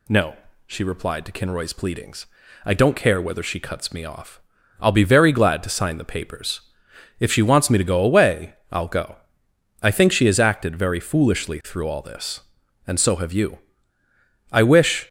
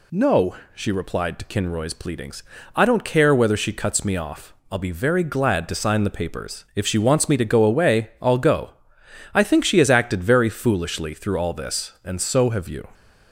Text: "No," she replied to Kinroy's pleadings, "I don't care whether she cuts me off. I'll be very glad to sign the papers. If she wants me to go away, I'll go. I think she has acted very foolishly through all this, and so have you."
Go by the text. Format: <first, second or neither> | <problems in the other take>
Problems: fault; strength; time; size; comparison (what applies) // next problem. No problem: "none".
second | goes on to say "I wish"; from 14.5 s on; 0.56 s long